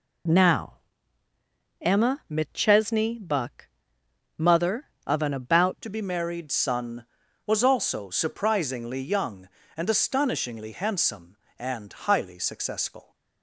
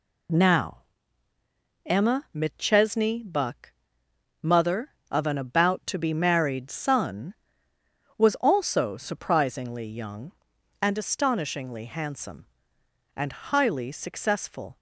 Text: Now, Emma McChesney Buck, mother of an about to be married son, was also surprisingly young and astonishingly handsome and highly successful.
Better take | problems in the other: second | changes voice at "to"; from 5.8 s on; 7.3 s long

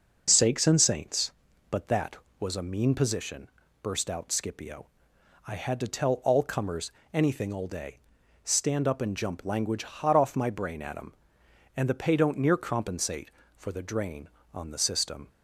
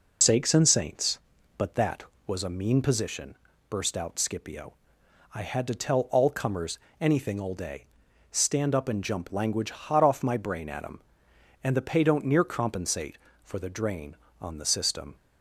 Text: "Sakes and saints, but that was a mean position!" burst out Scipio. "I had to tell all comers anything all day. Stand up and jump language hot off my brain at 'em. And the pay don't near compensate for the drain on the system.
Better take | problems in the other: first | loses the start of "Sakes"; at 0.2 s; 60 ms // pauses between "comers" and "anything"; slight; at 6.7 s; 0.24 s long; slight in the first

